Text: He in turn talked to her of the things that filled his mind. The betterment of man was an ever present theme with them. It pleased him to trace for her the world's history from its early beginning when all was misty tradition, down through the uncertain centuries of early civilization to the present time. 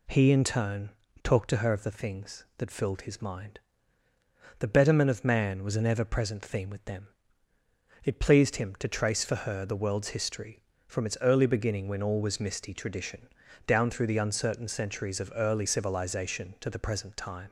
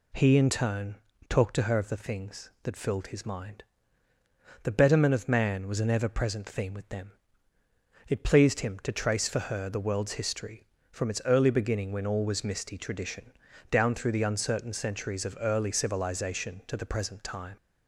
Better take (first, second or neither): neither